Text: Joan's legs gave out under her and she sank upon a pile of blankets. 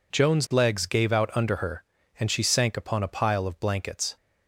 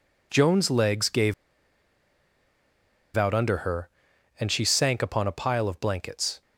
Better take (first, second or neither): first